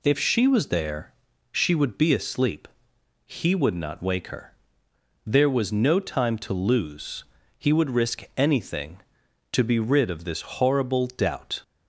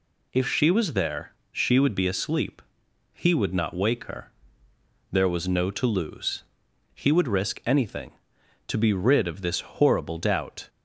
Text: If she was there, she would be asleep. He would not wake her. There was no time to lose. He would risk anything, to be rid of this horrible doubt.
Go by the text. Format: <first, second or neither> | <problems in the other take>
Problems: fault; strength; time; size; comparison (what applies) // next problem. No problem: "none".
first | skips "time"; at 5.7 s